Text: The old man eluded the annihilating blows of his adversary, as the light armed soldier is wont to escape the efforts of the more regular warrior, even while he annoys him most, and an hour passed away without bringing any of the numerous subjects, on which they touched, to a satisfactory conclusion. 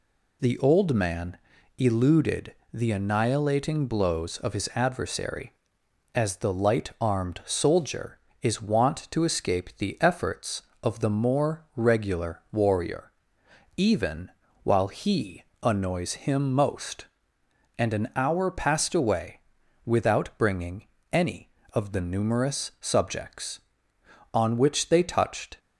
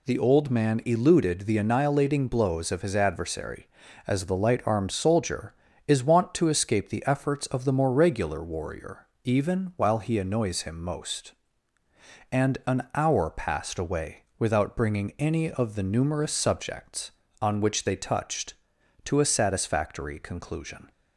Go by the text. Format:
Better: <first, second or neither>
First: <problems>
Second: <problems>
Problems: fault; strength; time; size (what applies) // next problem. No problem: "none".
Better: second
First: pauses between "man" and "eluded"; at 1.3 s; 0.40 s long // pauses between "eluded" and "the"; slight; at 2.5 s; 0.18 s long // pauses between "even" and "while"; slight; at 14.3 s; 0.32 s long // pauses between "he" and "annoys"; slight; at 15.4 s; 0.20 s long // pauses between "away" and "without"; at 19.4 s; 0.44 s long // pauses between "bringing" and "any"; slight; at 20.8 s; 0.26 s long // stops before "to a satisfactory conclusion"; at 25.5 s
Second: pauses between "away" and "without"; slight; at 14.2 s; 0.16 s long